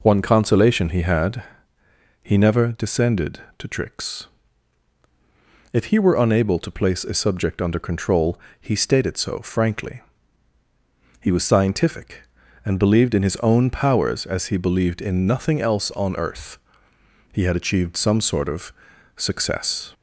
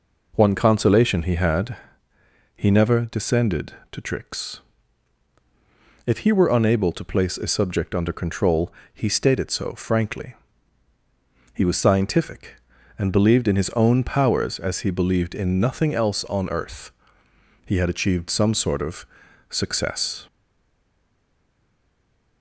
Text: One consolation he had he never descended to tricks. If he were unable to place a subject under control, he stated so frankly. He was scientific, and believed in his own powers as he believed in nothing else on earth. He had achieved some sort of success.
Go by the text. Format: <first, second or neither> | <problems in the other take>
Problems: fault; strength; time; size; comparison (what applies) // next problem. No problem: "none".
first | pauses between "had" and "he"; noticeable; at 1.7 s; 0.80 s long; noticeable in the first // pauses between "of" and "success"; at 19.0 s; 0.44 s long; also in the first // stays silent after the last word; from 20.2 s on; 2.2 s long